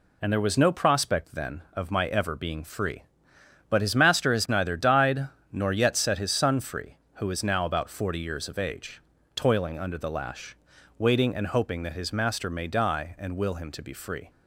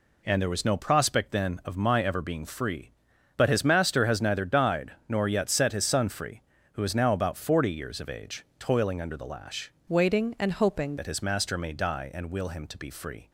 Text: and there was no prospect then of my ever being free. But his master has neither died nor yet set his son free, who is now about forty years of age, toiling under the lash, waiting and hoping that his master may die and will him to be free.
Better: first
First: pauses between "died" and "nor"; slight; at 5.2 s; 0.24 s long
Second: pauses between "died" and "nor"; slight; at 4.9 s; 0.18 s long // changes voice from "waiting" to "hoping"; from 9.8 to 10.9 s; 1.1 s long

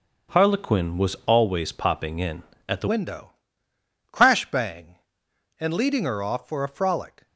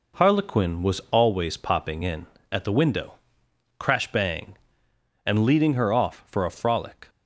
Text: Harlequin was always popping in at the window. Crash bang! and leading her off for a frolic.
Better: second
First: starts louder than the rest; until 1.4 s; 6.5 dB // changes voice at "window"; from 2.8 s on; 4.4 s long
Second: none

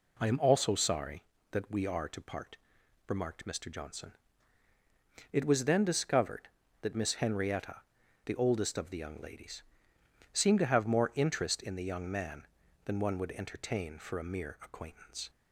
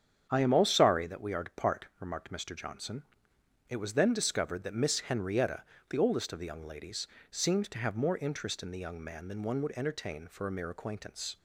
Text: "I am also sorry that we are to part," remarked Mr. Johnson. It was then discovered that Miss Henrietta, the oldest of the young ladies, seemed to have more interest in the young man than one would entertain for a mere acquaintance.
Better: first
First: none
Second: starts louder than the rest; strong; until 1.3 s; 8 dB // says "all" for "also"; at 0.5 s

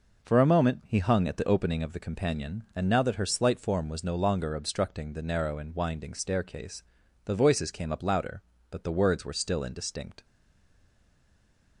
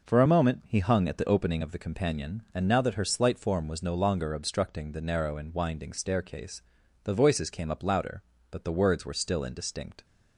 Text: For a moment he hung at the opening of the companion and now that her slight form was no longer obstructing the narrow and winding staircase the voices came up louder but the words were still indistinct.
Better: second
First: pauses between "staircase" and "the"; at 6.8 s; 0.42 s long // stays silent after the last word; noticeable; from 10.2 s on; 1.6 s long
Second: pauses between "staircase" and "the"; at 6.6 s; 0.42 s long

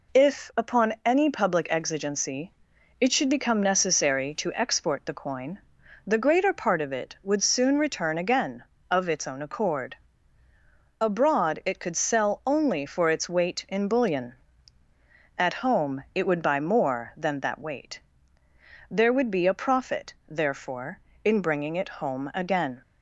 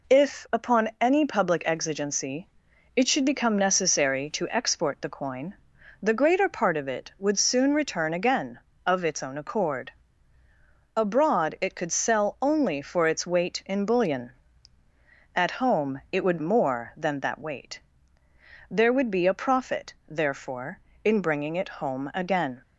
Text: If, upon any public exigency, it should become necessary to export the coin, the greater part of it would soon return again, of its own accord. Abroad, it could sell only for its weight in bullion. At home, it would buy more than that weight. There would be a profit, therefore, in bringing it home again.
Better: first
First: none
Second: skips "buy"; at 16.4 s

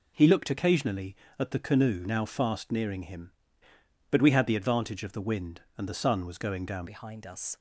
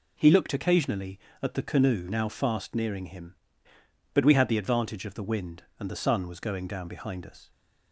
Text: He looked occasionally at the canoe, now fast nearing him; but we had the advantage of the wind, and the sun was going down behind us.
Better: second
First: changes voice at "behind"; from 6.8 s on; 0.7 s long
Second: none

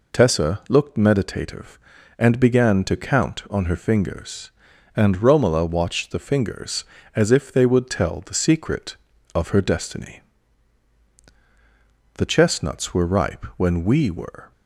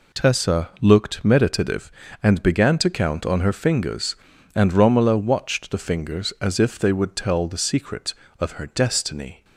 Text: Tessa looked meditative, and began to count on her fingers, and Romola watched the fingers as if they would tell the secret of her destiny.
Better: second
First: goes on to say "The chestnuts were ripe when we were"; strong; from 12.1 s on; 2.3 s long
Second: none

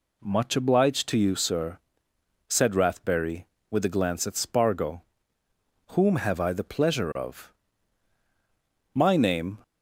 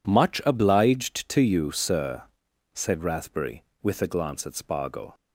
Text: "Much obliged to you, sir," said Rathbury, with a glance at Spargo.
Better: second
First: goes on to say "Whom have I the pleasure of My name"; strong; from 5.9 s on; 3.6 s long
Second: none

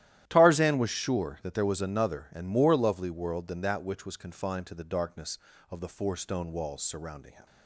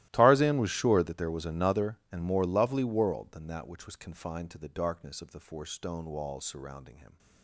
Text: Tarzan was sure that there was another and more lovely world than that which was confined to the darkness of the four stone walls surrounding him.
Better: first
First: starts louder than the rest; strong; until 1.2 s; 13 dB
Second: gets quieter; strong; throughout; 20 dB // starts louder than the rest; strong; until 1.1 s; 16 dB

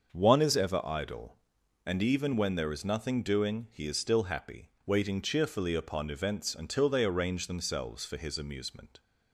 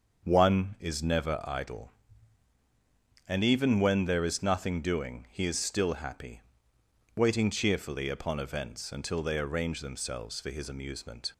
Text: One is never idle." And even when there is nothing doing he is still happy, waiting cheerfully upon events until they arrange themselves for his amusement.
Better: second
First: starts louder than the rest; until 1.1 s; 6.5 dB // says "ever" for "never"; at 0.5 s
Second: starts louder than the rest; until 1.2 s; 6.5 dB

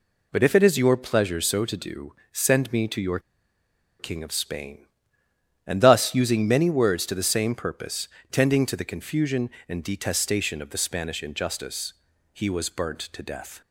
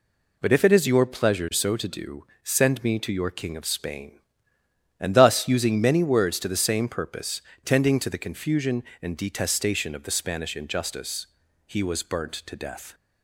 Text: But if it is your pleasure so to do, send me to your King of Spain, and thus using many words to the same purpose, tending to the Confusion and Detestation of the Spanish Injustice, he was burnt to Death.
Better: second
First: pauses between "your" and "King"; noticeable; at 3.1 s; 0.80 s long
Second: none

